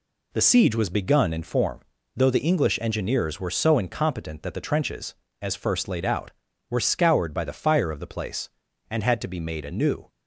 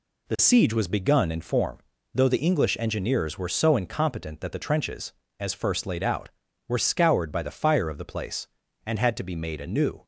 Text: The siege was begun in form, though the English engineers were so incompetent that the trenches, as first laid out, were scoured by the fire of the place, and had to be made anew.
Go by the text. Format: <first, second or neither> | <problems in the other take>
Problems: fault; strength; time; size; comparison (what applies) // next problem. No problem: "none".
neither | none